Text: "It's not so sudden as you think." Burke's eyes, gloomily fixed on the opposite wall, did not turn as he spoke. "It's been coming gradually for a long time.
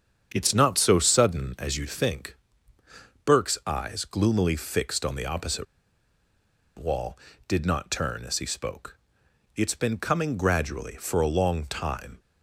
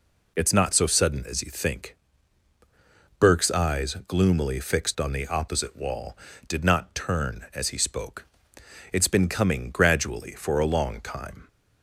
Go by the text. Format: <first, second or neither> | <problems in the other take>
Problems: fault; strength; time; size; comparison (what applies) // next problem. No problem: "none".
second | starts louder than the rest; strong; until 1.3 s; 7.5 dB // pauses between "opposite" and "wall"; at 5.6 s; 1.1 s long